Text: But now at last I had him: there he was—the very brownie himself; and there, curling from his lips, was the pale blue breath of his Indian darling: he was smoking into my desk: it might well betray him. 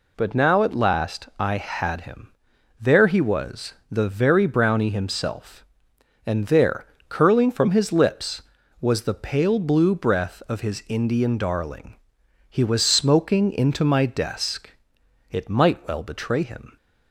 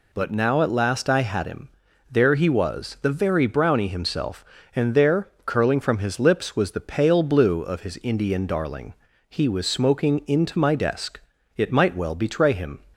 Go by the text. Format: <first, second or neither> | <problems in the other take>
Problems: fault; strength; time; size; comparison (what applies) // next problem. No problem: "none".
first | skips "breath"; at 7.6 s